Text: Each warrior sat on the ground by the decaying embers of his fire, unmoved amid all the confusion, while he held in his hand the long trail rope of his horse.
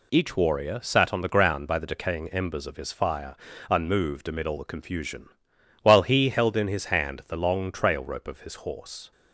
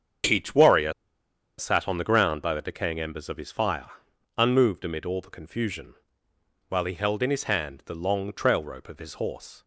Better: first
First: none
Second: starts louder than the rest; strong; until 1.9 s; 7.5 dB // pauses between "warrior" and "sat"; noticeable; at 0.9 s; 0.65 s long

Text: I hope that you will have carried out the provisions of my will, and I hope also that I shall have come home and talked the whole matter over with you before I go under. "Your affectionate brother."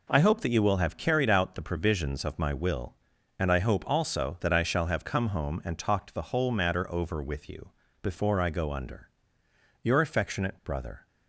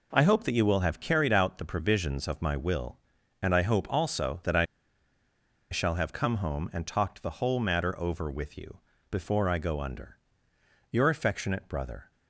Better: first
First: pauses between "you" and "before"; slight; at 7.7 s; 0.28 s long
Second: pauses between "I" and "shall"; at 4.6 s; 1.0 s long // pauses between "you" and "before"; slight; at 8.8 s; 0.28 s long

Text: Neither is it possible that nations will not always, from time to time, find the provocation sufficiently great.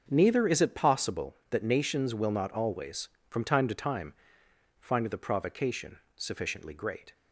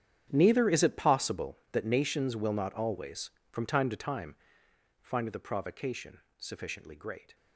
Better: first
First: starts louder than the rest; until 1.0 s; 6.5 dB // pauses between "provocation" and "sufficiently"; slight; at 5.9 s; 0.18 s long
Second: gets quieter; strong; throughout; 17 dB // starts louder than the rest; strong; until 1.3 s; 9.5 dB // pauses between "provocation" and "sufficiently"; slight; at 6.1 s; 0.18 s long

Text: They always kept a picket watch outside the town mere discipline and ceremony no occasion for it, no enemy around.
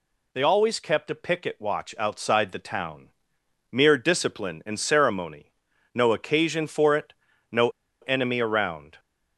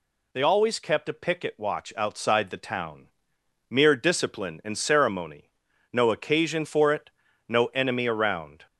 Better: second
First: pauses between "town" and "mere"; noticeable; at 3.0 s; 0.62 s long // pauses between "ceremony" and "no"; at 5.5 s; 0.42 s long // pauses between "no" and "enemy"; slight; at 7.6 s; 0.32 s long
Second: pauses between "town" and "mere"; noticeable; at 3.0 s; 0.62 s long // pauses between "ceremony" and "no"; at 5.4 s; 0.42 s long

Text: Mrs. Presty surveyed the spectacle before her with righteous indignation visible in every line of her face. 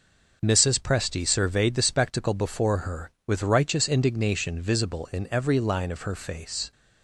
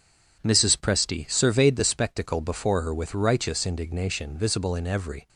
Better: first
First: none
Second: stops before "line of her face"; at 5.2 s

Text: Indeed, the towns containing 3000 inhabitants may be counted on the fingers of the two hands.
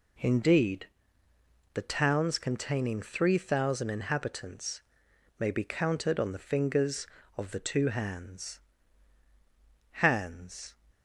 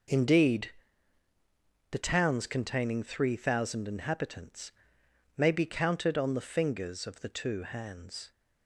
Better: second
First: pauses between "inhabitants" and "may"; noticeable; at 4.8 s; 0.58 s long // says "hands" twice; at 9.9 s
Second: pauses between "inhabitants" and "may"; noticeable; at 4.7 s; 0.66 s long

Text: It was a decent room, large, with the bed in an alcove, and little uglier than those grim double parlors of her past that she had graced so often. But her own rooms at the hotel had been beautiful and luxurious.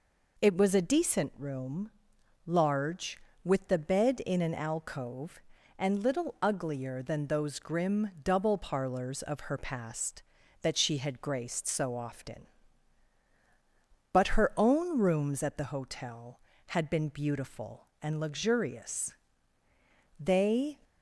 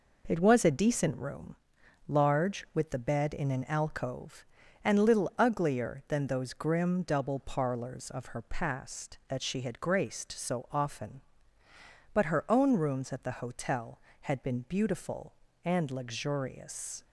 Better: second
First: goes on to say "They"; from 20.1 s on; 0.60 s long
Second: none

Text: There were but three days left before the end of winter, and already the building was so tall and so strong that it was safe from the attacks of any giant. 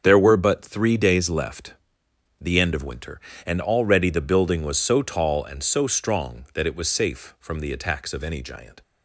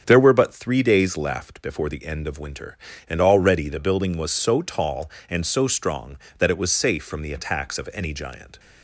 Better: second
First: starts louder than the rest; strong; until 1.0 s; 7 dB // skips "before"; at 2.0 s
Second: starts louder than the rest; strong; until 1.0 s; 7.5 dB

